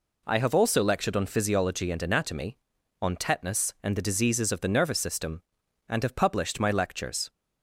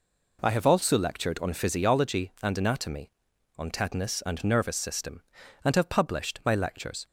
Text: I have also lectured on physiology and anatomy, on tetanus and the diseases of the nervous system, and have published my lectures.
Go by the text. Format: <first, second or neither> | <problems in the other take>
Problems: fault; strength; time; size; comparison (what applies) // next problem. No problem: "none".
first | skips "the diseases of the"; at 4.4 s